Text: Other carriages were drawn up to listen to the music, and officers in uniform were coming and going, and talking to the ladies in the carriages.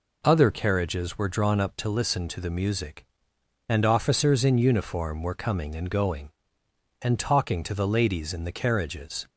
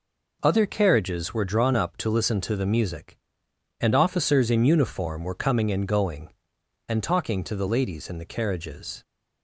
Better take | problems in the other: neither | none

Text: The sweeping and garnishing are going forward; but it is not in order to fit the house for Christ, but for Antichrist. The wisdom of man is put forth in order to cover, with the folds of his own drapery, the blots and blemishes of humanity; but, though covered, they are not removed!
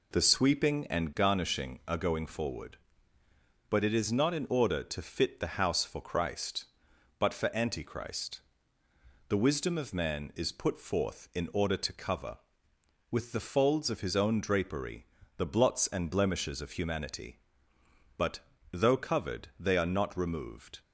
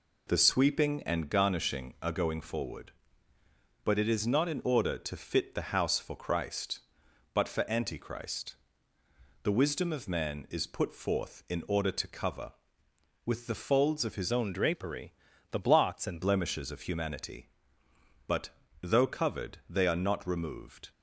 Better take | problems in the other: first | changes voice from "own" to "and"; from 14.2 to 16.2 s; 2.0 s long

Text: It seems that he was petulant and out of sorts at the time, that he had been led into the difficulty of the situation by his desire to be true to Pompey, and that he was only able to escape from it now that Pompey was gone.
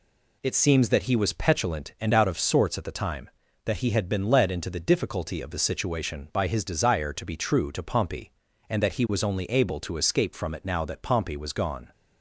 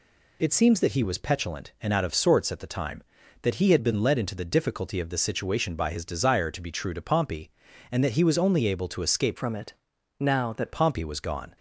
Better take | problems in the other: first | changes voice from "from" to "that"; from 9.3 to 10.7 s; 1.4 s long // pauses between "it" and "now"; at 9.7 s; 0.44 s long

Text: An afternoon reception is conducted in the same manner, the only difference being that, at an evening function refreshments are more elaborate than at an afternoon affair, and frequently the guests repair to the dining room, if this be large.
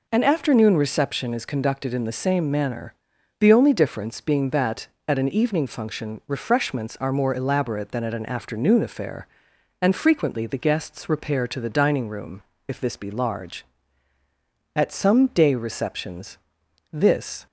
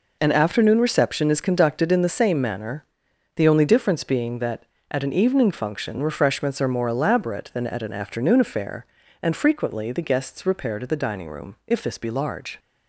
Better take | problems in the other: second | goes on to say "At some day receptions this"; strong; from 14.7 s on; 2.7 s long

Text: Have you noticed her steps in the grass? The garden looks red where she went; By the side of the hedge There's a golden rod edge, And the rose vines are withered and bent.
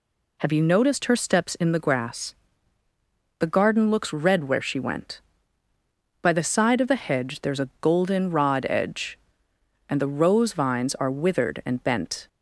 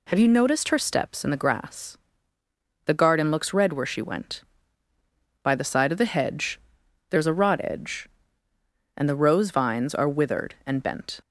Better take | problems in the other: first | pauses between "hedge" and "There's"; noticeable; at 6.6 s; 0.48 s long // skips "golden"; at 7.3 s

